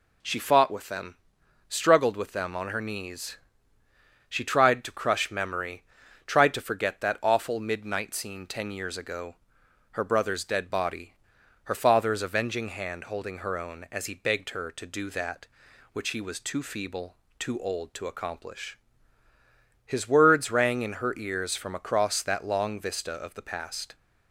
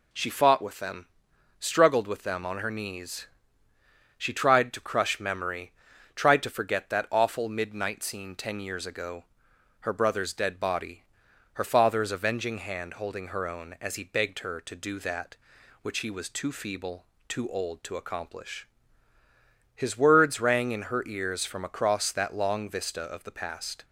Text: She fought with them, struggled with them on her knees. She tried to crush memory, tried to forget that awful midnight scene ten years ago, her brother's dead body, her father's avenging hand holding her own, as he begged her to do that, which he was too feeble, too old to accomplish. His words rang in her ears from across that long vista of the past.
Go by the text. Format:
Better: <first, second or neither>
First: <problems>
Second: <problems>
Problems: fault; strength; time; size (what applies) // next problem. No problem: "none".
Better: neither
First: none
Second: none